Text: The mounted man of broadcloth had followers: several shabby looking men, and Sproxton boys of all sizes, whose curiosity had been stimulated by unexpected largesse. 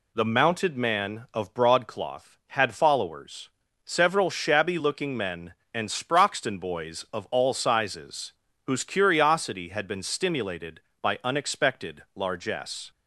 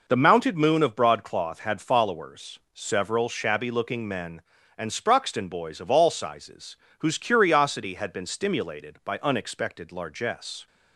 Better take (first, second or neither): first